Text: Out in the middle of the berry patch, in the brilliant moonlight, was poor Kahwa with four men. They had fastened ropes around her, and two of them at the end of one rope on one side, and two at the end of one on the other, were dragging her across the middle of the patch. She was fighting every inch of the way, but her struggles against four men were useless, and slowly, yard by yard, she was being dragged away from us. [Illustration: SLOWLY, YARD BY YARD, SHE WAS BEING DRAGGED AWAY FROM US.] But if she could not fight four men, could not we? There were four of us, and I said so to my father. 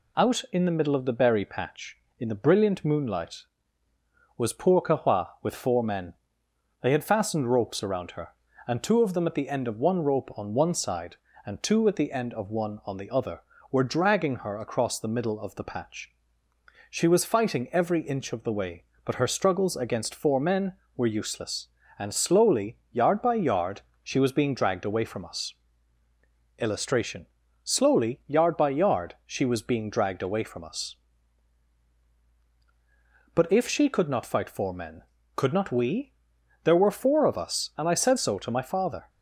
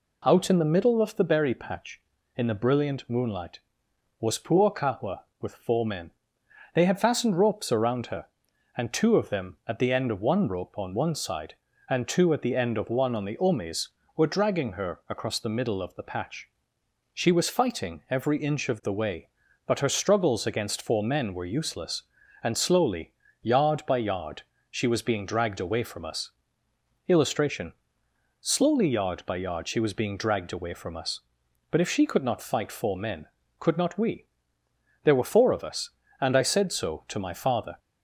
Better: first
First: none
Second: says "omes" for "other"; at 13.3 s

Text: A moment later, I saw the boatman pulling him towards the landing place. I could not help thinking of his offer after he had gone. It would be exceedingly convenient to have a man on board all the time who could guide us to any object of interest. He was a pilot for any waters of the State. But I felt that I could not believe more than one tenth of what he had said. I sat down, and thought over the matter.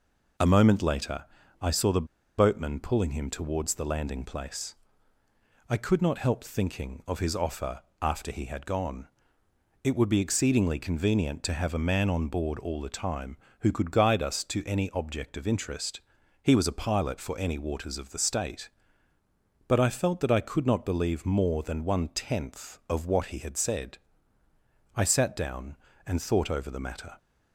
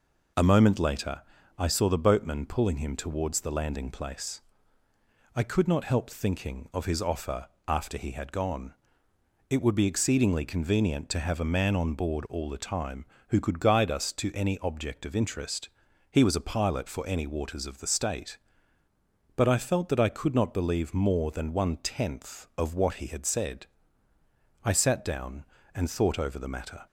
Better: second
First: pauses between "the" and "boatman"; slight; at 2.0 s; 0.32 s long // pauses between "offer" and "after"; slight; at 7.7 s; 0.22 s long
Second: pauses between "offer" and "after"; slight; at 7.4 s; 0.22 s long

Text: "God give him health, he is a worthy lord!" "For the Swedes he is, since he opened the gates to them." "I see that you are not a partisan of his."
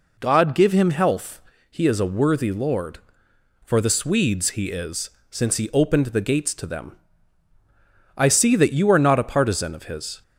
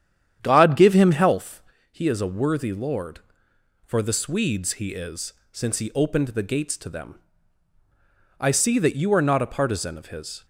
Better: first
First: none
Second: starts louder than the rest; strong; until 1.4 s; 9.5 dB

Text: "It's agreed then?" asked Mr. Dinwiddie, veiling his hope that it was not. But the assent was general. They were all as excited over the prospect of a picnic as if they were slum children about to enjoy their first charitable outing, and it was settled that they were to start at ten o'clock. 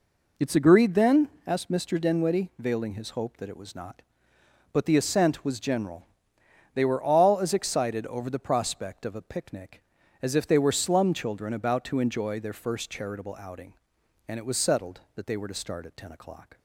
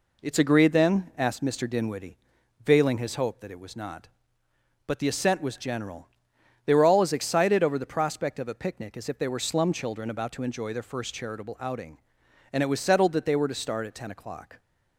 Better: neither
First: none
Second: none

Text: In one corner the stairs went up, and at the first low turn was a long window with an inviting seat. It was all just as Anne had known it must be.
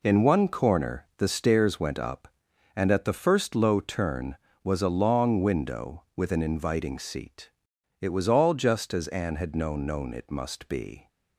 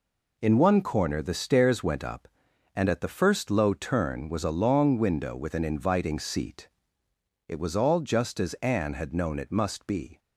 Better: second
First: says "known" twice; at 9.8 s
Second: none

